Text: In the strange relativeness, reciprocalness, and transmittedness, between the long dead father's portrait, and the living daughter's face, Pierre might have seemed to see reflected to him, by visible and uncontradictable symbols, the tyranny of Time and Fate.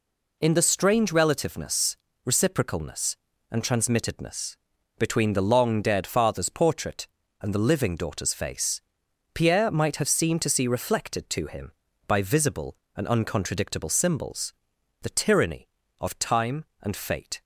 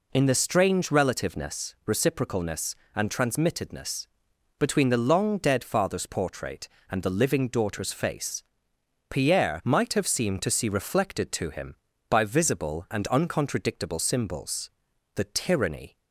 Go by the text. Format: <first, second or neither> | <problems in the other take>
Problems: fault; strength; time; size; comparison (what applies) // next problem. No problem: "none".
first | stops before "of Time and Fate"; at 15.9 s